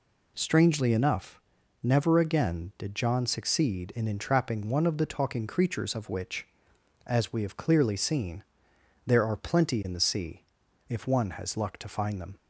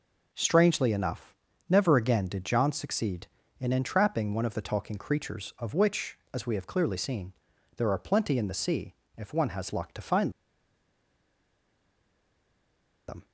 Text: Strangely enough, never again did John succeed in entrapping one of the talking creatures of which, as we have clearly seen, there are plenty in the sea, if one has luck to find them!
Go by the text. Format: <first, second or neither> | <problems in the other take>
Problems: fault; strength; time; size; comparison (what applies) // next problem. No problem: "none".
first | pauses between "find" and "them"; strong; at 10.3 s; 2.7 s long